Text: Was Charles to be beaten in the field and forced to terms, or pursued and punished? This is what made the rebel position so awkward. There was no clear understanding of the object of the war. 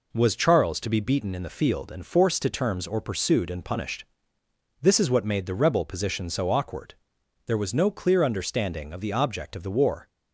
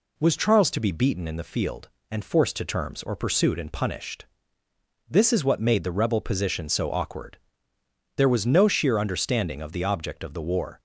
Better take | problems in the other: first | says "sheer" for "clear"; at 8.6 s

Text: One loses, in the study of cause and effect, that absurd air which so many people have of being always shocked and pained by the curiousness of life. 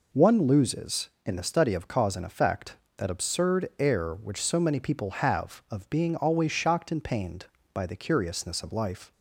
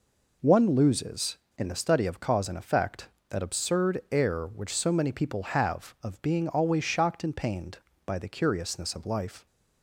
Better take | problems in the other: neither | none

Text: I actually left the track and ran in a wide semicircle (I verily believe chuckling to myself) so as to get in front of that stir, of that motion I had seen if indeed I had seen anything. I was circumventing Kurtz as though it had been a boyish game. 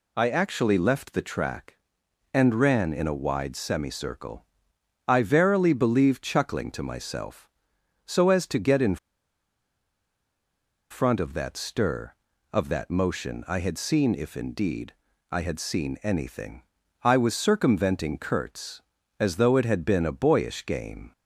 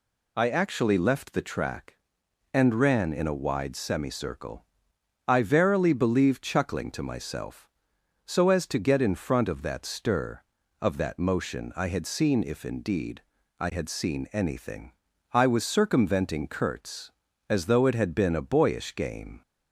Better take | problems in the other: second | pauses between "in" and "front"; strong; at 8.9 s; 1.9 s long // pauses between "indeed" and "I"; slight; at 14.9 s; 0.36 s long; slight in the second

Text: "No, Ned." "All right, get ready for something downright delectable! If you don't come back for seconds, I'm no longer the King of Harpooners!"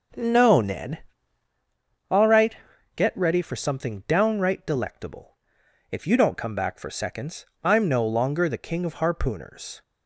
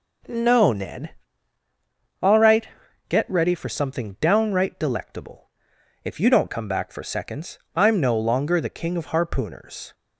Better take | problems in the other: second | starts louder than the rest; noticeable; until 1.7 s; 6 dB

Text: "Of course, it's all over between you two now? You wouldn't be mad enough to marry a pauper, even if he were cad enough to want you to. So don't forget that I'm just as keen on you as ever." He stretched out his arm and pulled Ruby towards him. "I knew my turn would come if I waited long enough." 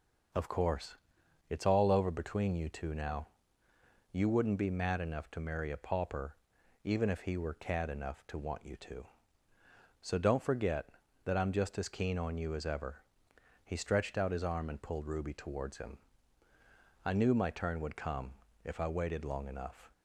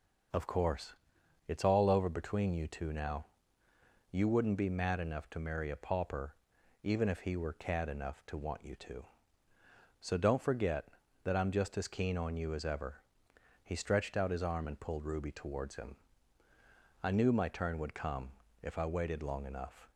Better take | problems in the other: neither | pauses between "come" and "if"; slight; the same in both

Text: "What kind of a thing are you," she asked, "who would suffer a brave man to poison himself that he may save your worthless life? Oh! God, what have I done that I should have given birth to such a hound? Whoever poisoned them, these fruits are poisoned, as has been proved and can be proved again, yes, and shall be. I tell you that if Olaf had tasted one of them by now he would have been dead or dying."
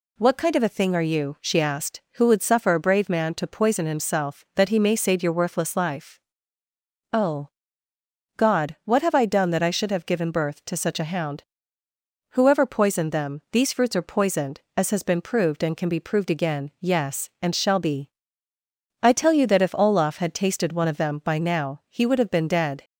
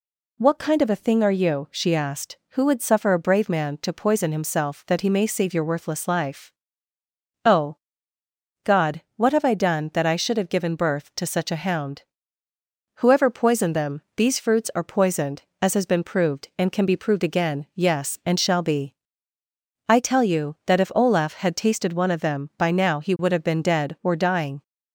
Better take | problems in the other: second | stops before "or dying"; at 22.8 s

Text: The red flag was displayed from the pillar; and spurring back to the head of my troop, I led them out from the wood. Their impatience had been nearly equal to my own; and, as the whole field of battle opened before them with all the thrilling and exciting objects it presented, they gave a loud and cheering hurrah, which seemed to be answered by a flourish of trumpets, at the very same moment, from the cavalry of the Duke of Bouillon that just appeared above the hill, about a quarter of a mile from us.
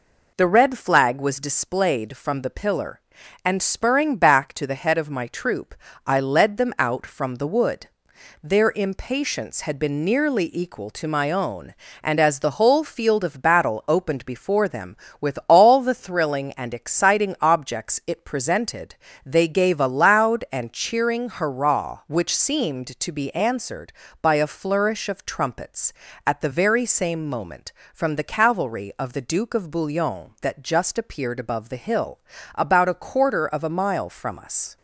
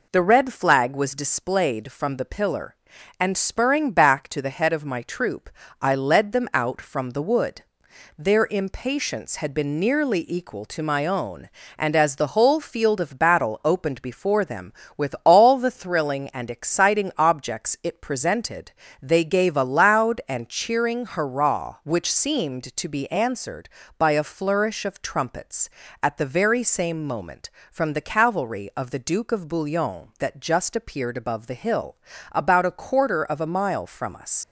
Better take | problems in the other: first | leaves "us" unfinished; at 34.4 s; 100 ms

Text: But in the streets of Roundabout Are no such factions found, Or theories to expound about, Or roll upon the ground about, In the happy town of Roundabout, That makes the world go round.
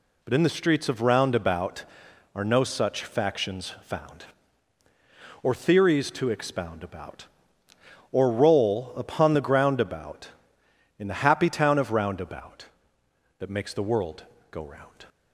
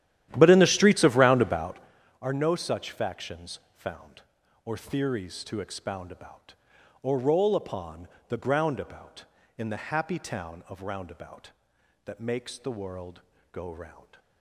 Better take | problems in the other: first | starts louder than the rest; strong; until 2.0 s; 12 dB // pauses between "factions" and "found"; slight; at 3.5 s; 0.16 s long // pauses between "upon" and "the"; slight; at 8.0 s; 0.20 s long // pauses between "world" and "go"; slight; at 13.2 s; 0.32 s long; slight in the first

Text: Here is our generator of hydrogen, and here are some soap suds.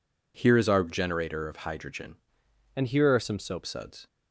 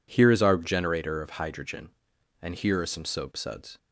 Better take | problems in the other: second | changes voice from "and" to "soap"; from 2.7 to 3.6 s; 0.9 s long

